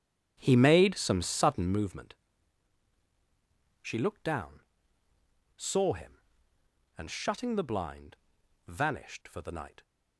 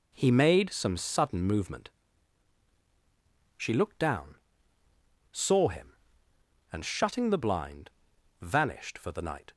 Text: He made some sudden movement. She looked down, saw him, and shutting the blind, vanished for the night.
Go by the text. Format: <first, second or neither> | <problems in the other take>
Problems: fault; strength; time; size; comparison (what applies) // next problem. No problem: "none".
second | starts louder than the rest; strong; until 1.9 s; 9 dB